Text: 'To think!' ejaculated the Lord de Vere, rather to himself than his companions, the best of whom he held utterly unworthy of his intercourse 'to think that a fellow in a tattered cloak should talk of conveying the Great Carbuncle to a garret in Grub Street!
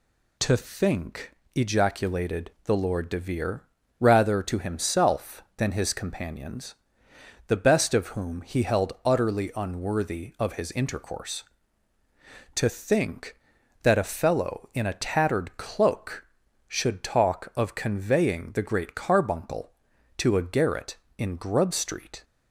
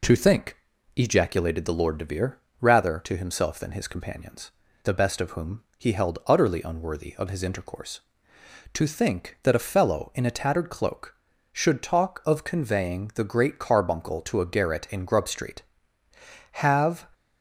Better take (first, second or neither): first